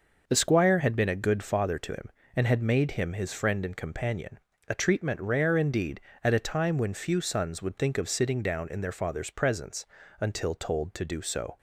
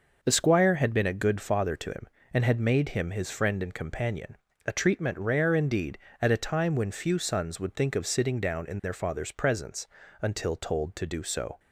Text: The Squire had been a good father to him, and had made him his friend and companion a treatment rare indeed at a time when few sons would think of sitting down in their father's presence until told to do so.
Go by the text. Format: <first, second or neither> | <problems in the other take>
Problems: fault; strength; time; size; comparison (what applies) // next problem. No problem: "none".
neither | pauses between "companion" and "a"; slight; the same in both // pauses between "presence" and "until"; the same in both